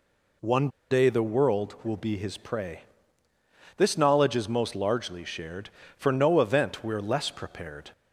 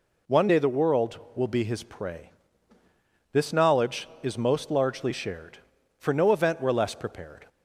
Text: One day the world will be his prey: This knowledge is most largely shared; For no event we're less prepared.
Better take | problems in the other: second | pauses between "One" and "day"; slight; at 0.6 s; 0.21 s long

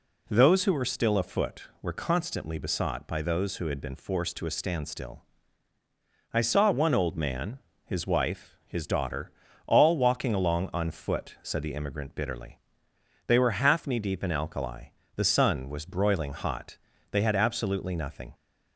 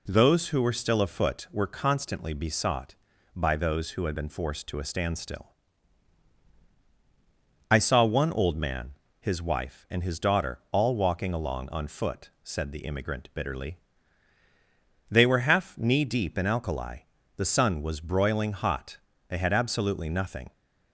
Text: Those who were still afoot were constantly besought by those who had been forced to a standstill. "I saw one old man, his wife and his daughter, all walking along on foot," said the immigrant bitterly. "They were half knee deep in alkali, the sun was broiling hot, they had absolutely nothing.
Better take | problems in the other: second | skips "and"; at 8.6 s

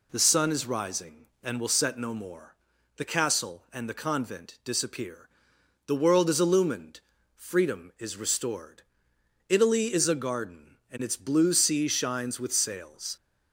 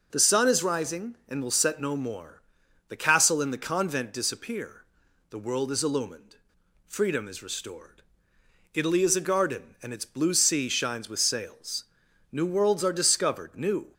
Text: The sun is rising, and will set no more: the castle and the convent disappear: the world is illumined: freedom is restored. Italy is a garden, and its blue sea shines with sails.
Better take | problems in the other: first | goes on to say "New worlds are discovered new"; from 12.3 s on; 1.6 s long

